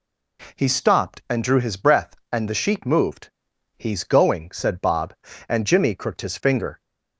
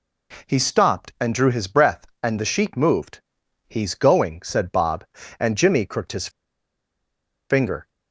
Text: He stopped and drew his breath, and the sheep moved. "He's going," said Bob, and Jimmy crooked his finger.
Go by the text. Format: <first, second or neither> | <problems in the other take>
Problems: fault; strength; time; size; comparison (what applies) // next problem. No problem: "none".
first | pauses between "his" and "finger"; at 6.2 s; 1.2 s long